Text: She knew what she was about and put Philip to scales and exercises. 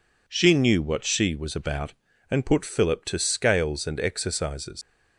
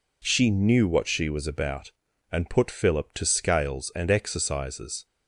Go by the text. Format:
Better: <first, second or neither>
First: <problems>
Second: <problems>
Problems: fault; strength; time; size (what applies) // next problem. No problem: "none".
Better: second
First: leaves "exercises" unfinished; at 4.8 s; 70 ms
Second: none